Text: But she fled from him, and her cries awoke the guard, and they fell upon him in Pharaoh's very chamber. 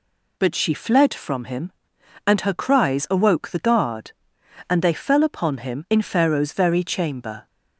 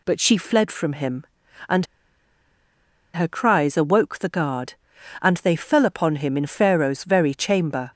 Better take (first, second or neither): first